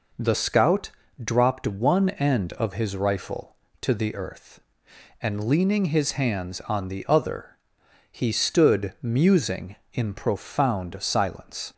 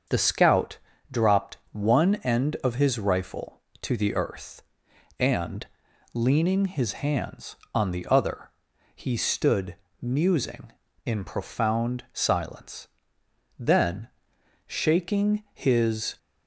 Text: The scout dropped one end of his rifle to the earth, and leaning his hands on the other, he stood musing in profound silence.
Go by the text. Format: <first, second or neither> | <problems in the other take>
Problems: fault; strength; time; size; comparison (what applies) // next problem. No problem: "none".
first | starts louder than the rest; until 1.4 s; 7 dB // pauses between "scout" and "dropped"; slight; at 0.7 s; 0.34 s long; slight in the first // pauses between "and" and "leaning"; noticeable; at 5.6 s; 0.48 s long // pauses between "stood" and "musing"; slight; at 9.7 s; 0.24 s long // goes on to say "Then shaking his"; strong; from 13.5 s on; 2.5 s long